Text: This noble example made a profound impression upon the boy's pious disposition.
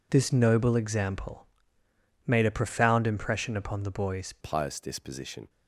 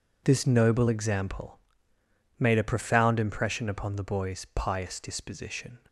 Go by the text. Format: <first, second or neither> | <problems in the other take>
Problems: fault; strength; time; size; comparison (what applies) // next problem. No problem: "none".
second | pauses between "example" and "made"; noticeable; at 1.4 s; 0.80 s long; noticeable in the second // changes voice at "pious"; from 4.3 s on; 1.1 s long